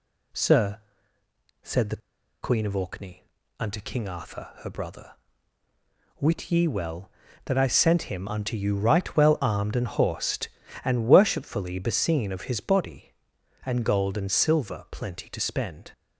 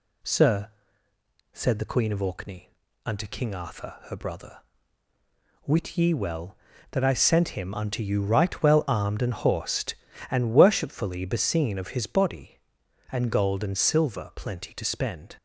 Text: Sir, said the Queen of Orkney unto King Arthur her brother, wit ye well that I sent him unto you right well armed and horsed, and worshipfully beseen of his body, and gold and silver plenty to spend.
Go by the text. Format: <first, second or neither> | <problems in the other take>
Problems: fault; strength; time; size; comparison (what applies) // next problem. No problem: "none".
second | pauses between "the" and "Queen"; at 2.0 s; 0.43 s long // pauses between "Orkney" and "unto"; slight; at 3.2 s; 0.36 s long; slight in the second